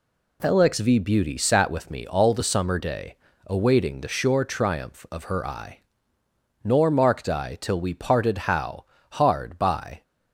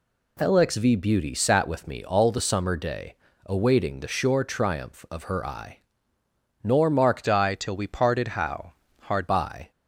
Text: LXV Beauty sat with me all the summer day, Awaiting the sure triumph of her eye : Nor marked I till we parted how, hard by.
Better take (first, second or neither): first